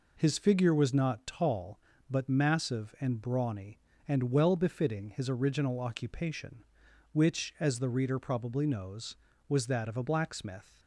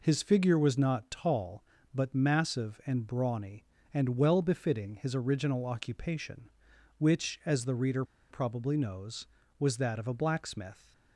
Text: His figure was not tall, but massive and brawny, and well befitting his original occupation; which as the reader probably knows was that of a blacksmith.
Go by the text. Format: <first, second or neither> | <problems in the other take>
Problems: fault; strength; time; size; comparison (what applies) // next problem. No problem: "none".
first | pauses between "reader" and "probably"; slight; at 8.0 s; 0.27 s long